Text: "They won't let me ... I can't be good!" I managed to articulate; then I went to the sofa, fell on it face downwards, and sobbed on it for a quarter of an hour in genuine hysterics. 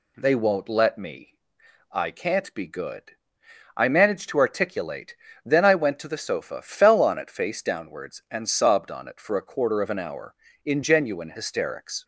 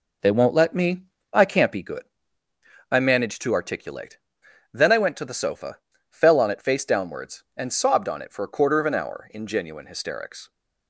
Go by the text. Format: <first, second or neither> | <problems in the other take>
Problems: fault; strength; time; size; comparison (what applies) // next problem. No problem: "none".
first | starts louder than the rest; noticeable; until 1.9 s; 4.5 dB